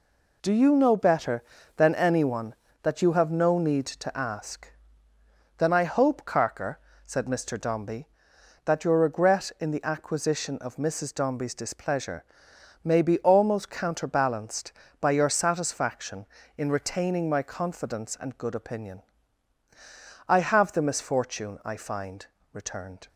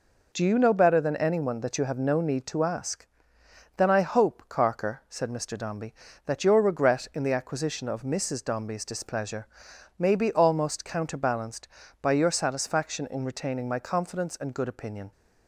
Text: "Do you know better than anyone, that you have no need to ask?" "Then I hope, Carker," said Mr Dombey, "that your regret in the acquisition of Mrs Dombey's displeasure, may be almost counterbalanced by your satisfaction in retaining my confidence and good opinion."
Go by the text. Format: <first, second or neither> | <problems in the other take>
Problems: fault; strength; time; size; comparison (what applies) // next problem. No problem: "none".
second | goes on to say "I have the misfortune I find returned"; strong; from 20.2 s on; 2.8 s long